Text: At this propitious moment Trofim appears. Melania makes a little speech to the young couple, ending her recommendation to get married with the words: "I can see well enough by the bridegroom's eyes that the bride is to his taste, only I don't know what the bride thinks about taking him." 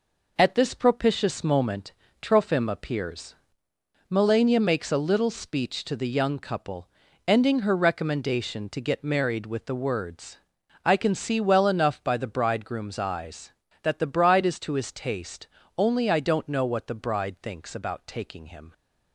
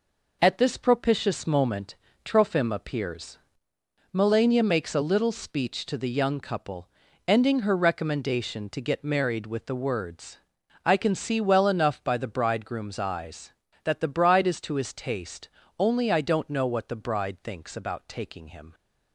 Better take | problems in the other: neither | pauses between "moment" and "Trofim"; slight; the same in both

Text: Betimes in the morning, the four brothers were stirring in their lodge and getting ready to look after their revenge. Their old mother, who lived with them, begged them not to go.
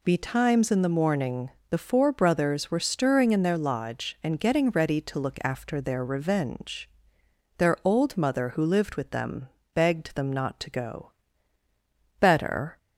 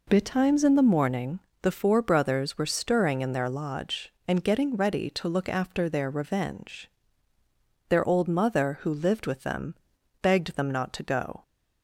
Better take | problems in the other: second | goes on to say "Better"; from 12.1 s on; 0.60 s long

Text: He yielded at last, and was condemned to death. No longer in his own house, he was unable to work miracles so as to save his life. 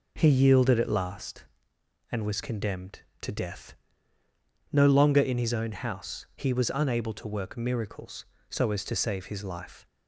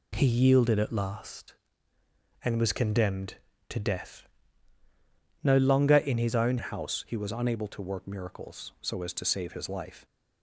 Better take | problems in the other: first | changes voice at "house"; from 6.5 s on; 3.5 s long

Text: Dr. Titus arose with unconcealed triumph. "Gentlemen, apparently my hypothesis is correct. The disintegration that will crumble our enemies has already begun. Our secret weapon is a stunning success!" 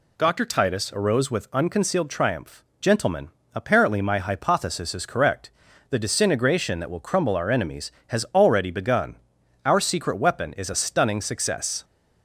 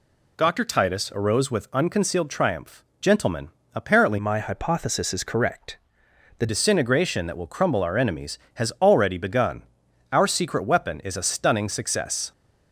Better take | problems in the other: first | changes voice from "my" to "The"; from 4.1 to 6.4 s; 2.3 s long

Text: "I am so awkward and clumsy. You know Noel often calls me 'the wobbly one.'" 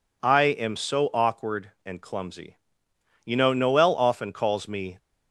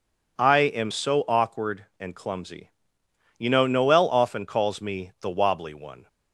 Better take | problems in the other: second | stops before "the wobbly one"; at 4.9 s

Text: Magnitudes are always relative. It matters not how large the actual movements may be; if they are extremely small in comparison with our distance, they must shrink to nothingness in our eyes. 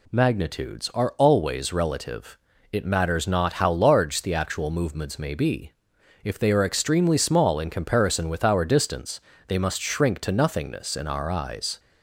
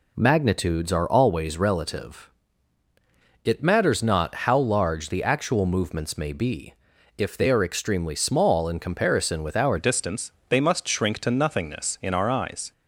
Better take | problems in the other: first | changes voice at "distance"; from 9.7 s on; 3.0 s long

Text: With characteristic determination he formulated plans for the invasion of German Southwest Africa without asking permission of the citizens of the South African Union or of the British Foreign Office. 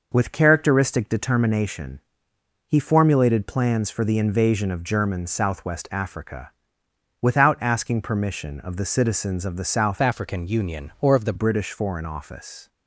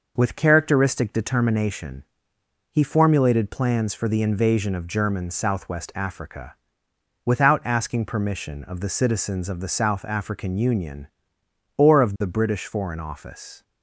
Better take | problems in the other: second | pauses between "determination" and "he"; noticeable; at 1.9 s; 0.68 s long; noticeable in the second // pauses between "Africa" and "without"; noticeable; at 6.5 s; 0.72 s long; noticeable in the second // changes voice from "African" to "the"; from 10.0 to 11.3 s; 1.3 s long

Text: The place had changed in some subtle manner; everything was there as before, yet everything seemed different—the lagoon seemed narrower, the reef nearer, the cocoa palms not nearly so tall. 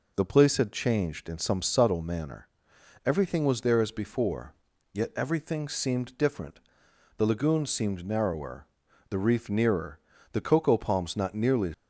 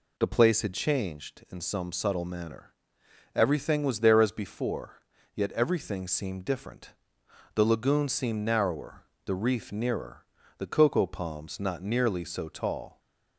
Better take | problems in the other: second | stops before "so tall"; at 11.7 s

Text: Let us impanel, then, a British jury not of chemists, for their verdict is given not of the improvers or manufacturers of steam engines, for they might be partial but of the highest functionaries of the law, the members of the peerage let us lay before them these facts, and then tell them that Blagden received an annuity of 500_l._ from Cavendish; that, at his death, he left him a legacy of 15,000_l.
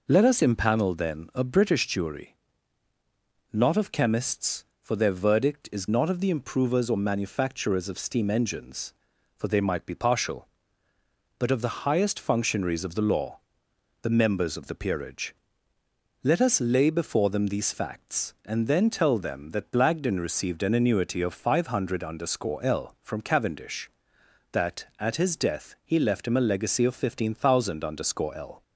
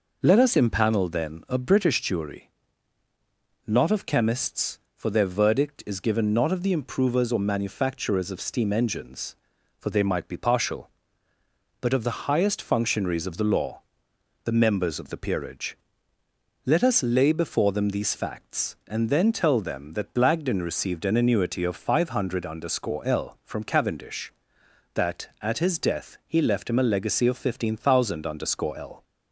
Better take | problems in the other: second | pauses between "jury" and "not"; at 2.3 s; 1.2 s long; also in the second // skips "given"; at 5.8 s // pauses between "peerage" and "let"; noticeable; at 15.3 s; 0.88 s long; noticeable in the second

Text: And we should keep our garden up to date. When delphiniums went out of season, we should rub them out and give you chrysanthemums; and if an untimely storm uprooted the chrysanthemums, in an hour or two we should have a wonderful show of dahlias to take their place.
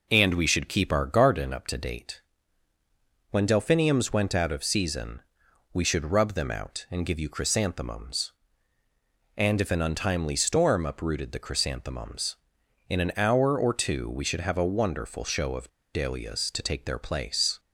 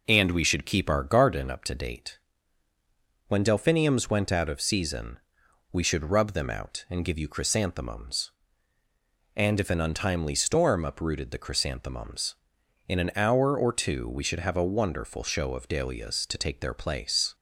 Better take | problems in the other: second | pauses between "of" and "dahlias"; slight; at 15.6 s; 0.25 s long

